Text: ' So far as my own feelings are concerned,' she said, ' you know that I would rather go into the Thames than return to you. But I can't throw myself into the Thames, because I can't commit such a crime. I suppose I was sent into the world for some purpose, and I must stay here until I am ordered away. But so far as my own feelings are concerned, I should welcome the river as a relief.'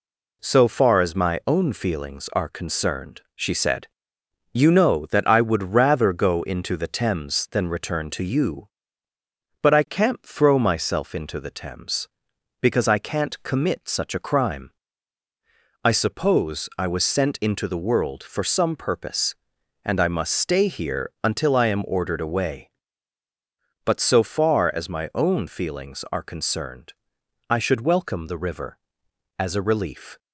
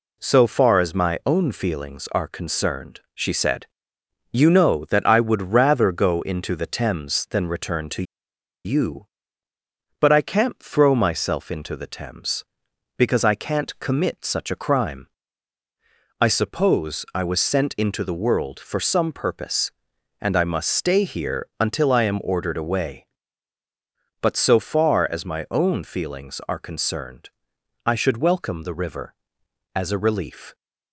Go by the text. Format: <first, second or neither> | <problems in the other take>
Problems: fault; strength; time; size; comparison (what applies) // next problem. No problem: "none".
first | pauses between "to" and "you"; noticeable; at 8.0 s; 0.61 s long